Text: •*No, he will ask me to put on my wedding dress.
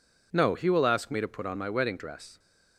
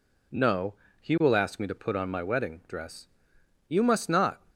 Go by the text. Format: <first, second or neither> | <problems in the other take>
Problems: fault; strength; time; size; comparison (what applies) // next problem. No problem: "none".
first | goes on to say "You must not"; noticeable; from 3.6 s on; 0.72 s long